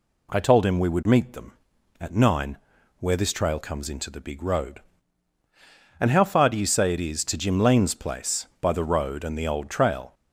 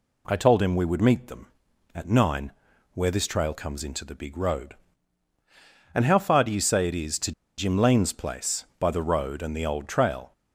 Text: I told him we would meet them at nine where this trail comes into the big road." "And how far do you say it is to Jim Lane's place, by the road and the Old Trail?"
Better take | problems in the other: first | pauses between "nine" and "where"; at 2.5 s; 0.42 s long; also in the first // pauses between "to" and "Jim"; slight; at 7.3 s; 0.25 s long

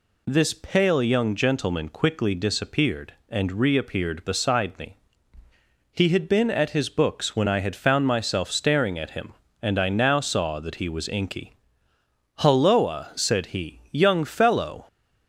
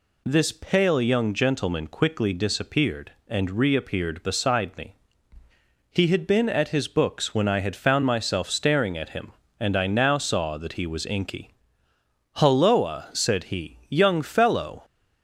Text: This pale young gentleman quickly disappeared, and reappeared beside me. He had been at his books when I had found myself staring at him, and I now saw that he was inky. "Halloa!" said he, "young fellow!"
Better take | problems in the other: neither | none

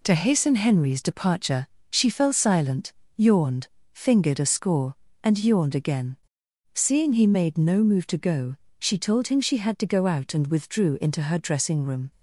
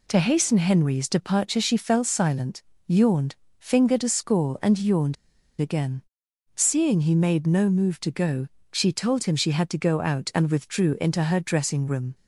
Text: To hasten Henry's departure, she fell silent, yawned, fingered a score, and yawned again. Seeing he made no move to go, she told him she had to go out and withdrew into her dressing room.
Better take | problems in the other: first | pauses between "yawned" and "again"; at 5.1 s; 0.45 s long

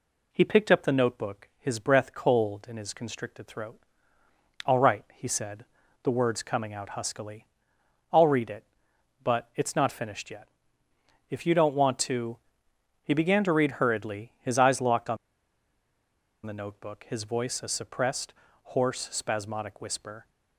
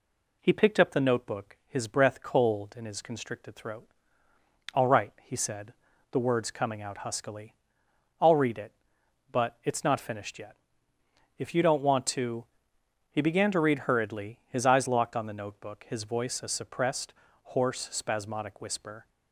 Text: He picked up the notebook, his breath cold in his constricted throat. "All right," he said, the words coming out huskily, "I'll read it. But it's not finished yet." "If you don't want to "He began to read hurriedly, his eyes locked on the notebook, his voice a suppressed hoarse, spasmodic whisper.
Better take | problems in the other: second | pauses between "to" and "He"; noticeable; at 12.3 s; 0.66 s long; noticeable in the second // pauses between "on" and "the"; strong; at 15.1 s; 1.2 s long // pauses between "suppressed" and "hoarse"; slight; at 18.3 s; 0.30 s long; slight in the second

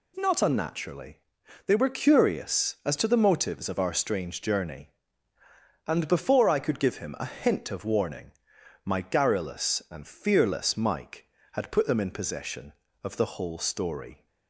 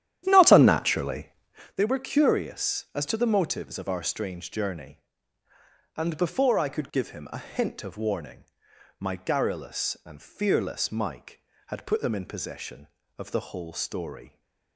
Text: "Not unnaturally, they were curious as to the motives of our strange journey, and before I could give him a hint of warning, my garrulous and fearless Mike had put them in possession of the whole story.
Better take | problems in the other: first | starts louder than the rest; strong; until 1.8 s; 11 dB

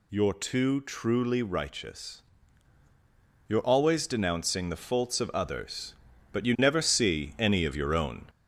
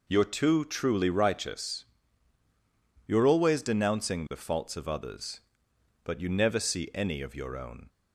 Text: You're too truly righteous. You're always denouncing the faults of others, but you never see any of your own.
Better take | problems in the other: second | gets louder; slight; throughout; 3 dB

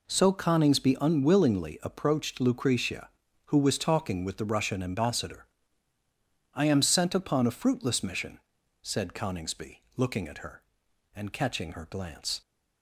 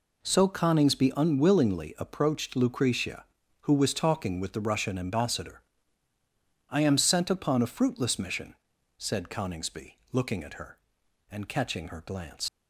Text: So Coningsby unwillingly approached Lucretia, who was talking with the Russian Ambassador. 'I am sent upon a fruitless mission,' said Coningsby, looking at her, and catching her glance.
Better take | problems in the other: first | leaves "glance" unfinished; at 12.4 s; 80 ms

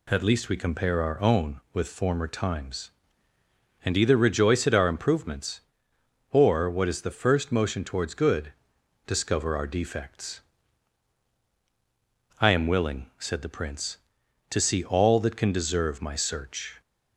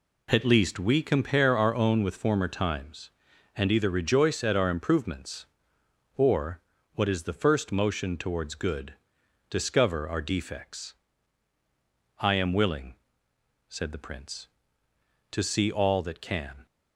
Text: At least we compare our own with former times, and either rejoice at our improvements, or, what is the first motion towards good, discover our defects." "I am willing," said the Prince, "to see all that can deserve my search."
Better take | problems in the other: first | stops before "deserve my search"; at 16.6 s

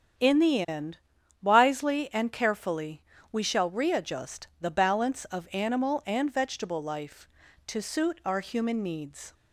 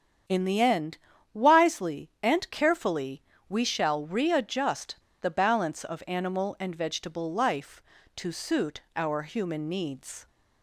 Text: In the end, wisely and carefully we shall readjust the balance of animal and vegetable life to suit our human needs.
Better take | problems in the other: first | starts louder than the rest; strong; until 1.6 s; 8 dB; strong in the first // pauses between "carefully" and "we"; slight; at 3.2 s; 0.26 s long; slight in the first // pauses between "readjust" and "the"; slight; at 4.9 s; 0.25 s long

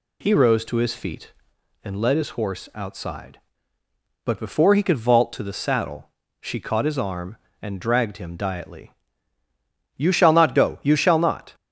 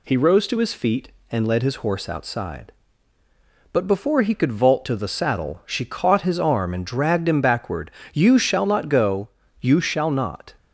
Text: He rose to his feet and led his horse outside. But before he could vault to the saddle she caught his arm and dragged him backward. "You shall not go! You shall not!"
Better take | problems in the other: second | pauses between "saddle" and "she"; slight; at 6.0 s; 0.30 s long // says "diately" for "backward"; at 8.3 s

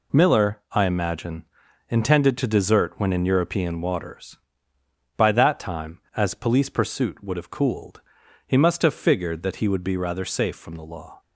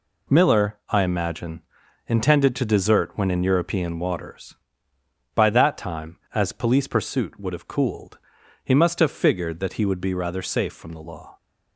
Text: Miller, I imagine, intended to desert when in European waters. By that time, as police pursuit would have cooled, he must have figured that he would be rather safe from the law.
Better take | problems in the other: neither | none

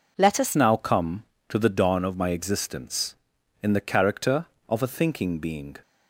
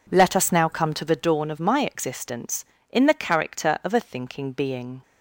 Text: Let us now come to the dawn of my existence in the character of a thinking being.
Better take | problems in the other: second | changes voice at "now"; from 0.5 s on; 5.2 s long

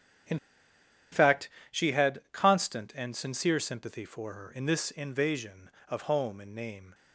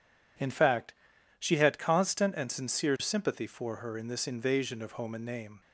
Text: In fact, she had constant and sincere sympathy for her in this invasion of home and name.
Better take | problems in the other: second | starts louder than the rest; strong; until 2.3 s; 8.5 dB // pauses between "In" and "fact"; noticeable; at 0.3 s; 0.74 s long

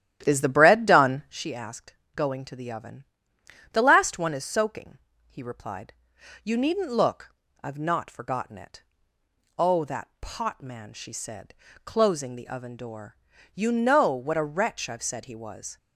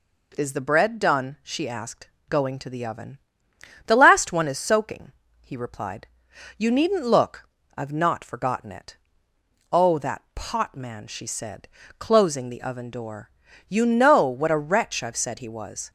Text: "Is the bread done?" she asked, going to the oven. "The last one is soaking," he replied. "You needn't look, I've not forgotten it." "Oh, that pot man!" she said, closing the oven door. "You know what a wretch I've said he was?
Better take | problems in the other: second | starts louder than the rest; strong; until 1.4 s; 11.5 dB

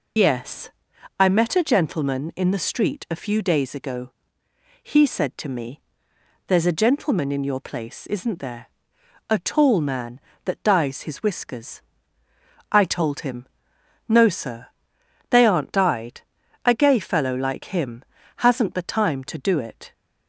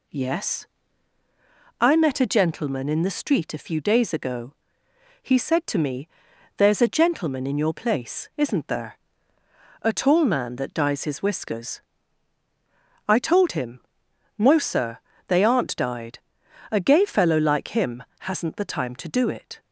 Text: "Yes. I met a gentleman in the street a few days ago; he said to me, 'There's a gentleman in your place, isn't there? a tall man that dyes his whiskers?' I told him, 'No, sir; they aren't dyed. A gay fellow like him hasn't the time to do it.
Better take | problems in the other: second | loses the start of "Yes"; at 0.1 s; 75 ms // pauses between "him" and "hasn't"; slight; at 18.0 s; 0.36 s long; slight in the second

